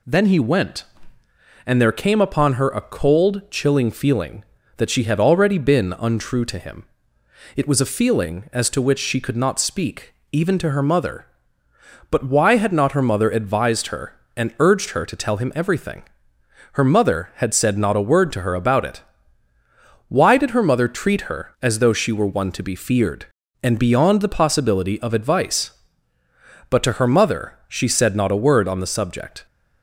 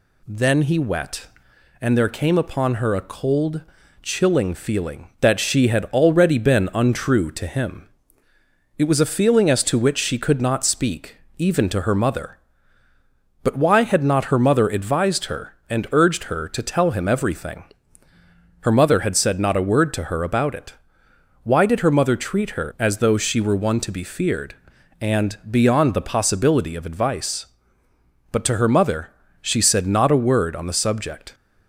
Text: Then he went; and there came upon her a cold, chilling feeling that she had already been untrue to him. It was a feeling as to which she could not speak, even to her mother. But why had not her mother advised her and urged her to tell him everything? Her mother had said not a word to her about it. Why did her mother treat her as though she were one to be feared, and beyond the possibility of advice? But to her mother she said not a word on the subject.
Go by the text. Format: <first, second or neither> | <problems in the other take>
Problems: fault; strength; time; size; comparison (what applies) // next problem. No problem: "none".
first | says "wet" for "went"; at 0.7 s // pauses between "mother" and "she"; slight; at 29.1 s; 0.32 s long; slight in the first